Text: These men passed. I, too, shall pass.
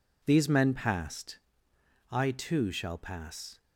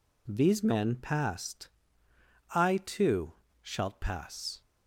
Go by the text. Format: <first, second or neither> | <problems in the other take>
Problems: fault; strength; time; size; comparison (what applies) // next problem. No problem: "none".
first | says "shalt" for "shall"; at 3.6 s